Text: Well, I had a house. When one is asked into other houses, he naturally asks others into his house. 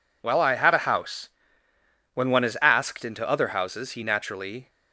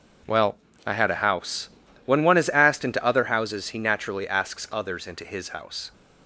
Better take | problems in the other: second | stops before "asks others into his house"; at 4.6 s

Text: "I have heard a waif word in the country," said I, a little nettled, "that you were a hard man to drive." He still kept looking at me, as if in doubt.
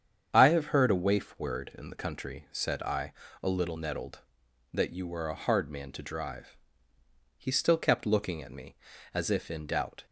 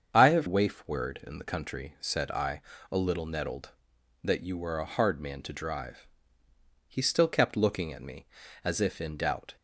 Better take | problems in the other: first | starts louder than the rest; strong; until 1.1 s; 7 dB; strong in the first // skips "heard a"; at 0.4 s

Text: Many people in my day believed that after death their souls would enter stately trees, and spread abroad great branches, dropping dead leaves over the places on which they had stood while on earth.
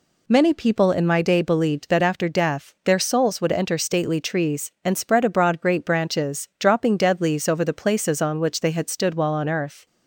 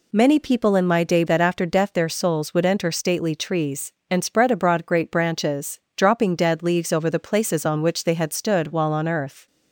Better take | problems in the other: first | skips "believed"; at 1.2 s

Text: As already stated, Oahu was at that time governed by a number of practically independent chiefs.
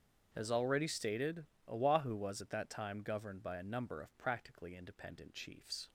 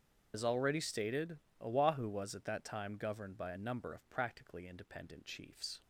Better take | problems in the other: first | loses the start of "As"; at 0.3 s; 75 ms // starts louder than the rest; until 1.3 s; 7 dB; strong in the first

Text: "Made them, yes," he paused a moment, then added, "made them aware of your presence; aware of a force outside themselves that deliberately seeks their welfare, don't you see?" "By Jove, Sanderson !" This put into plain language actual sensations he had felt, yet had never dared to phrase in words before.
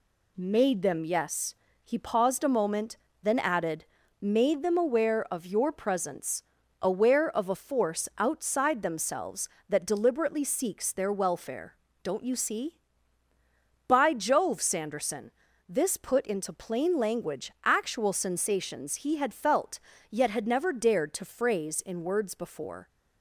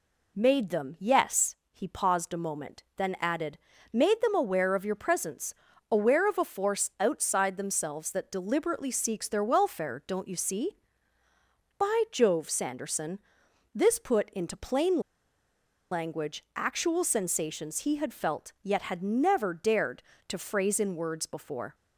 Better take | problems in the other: first | pauses between "plain" and "language"; noticeable; at 14.9 s; 0.91 s long

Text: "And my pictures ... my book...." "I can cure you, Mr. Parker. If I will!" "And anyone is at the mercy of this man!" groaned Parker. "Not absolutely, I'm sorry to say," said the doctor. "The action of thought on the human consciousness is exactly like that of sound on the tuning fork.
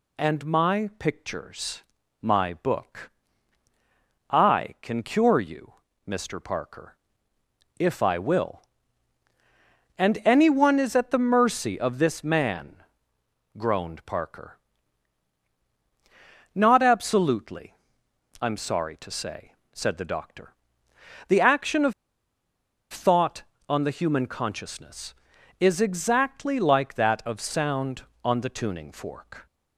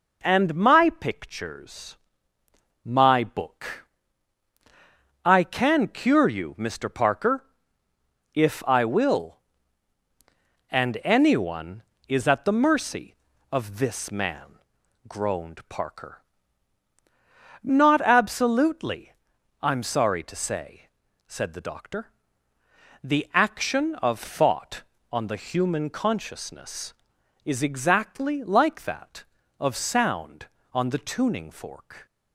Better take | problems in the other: second | pauses between "of" and "thought"; at 21.9 s; 1.0 s long

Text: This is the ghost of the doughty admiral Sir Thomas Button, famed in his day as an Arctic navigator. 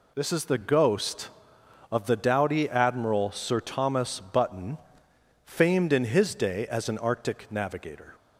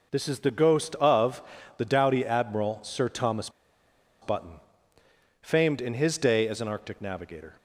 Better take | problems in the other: first | pauses between "of" and "the"; slight; at 1.4 s; 0.34 s long // pauses between "Thomas" and "Button"; noticeable; at 3.4 s; 0.72 s long

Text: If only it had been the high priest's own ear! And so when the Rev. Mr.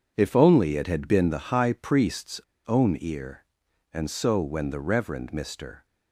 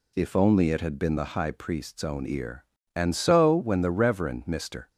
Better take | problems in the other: second | pauses between "priest's" and "own"; slight; at 2.4 s; 0.26 s long

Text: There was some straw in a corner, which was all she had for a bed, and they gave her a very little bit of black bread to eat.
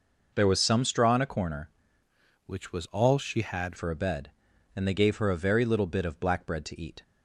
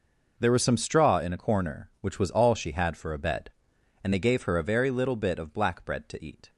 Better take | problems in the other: second | changes voice from "which" to "had"; from 2.4 to 3.7 s; 1.3 s long

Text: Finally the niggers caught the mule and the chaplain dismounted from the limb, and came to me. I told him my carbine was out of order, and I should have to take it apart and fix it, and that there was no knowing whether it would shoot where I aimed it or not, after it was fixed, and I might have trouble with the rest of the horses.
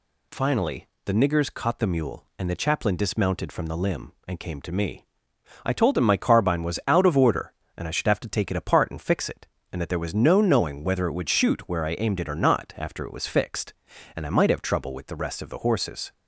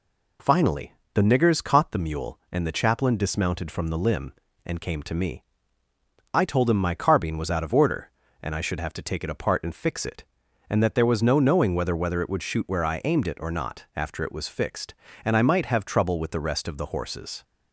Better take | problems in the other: first | pauses between "Finally" and "the"; slight; at 0.9 s; 0.22 s long; slight in the first // says "whether" twice; at 11.9 s

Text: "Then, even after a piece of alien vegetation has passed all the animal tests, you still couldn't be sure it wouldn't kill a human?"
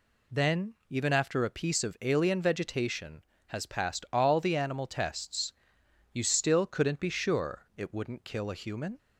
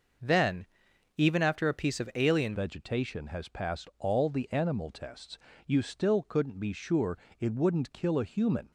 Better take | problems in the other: first | changes voice at "vegetation"; from 2.5 s on; 6.2 s long // pauses between "sure" and "it"; slight; at 7.1 s; 0.20 s long

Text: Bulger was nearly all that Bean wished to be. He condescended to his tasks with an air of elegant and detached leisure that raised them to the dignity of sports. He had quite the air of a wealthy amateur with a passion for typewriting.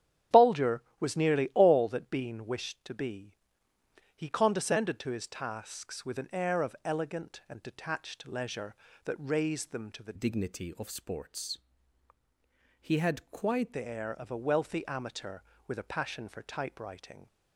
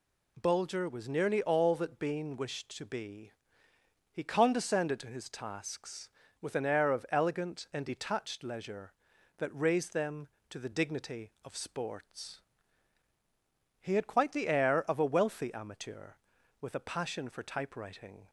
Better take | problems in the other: second | starts louder than the rest; strong; until 1.4 s; 9.5 dB // changes voice from "dignity" to "quite"; from 10.1 to 13.7 s; 3.6 s long

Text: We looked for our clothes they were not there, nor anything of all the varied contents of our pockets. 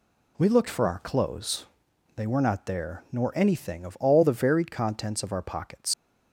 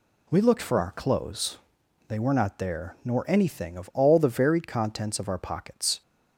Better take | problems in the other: second | pauses between "clothes" and "they"; noticeable; at 1.6 s; 0.52 s long; noticeable in the second // leaves "pockets" unfinished; at 5.9 s; 115 ms

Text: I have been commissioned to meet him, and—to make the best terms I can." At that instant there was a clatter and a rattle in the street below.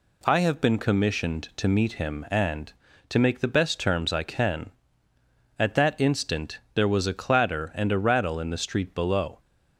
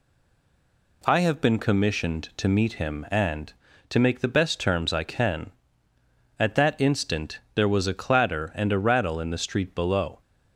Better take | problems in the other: first | stays silent before the first word; until 1.0 s; 1.0 s long // pauses between "instant" and "there"; slight; at 7.4 s; 0.16 s long; slight in the first

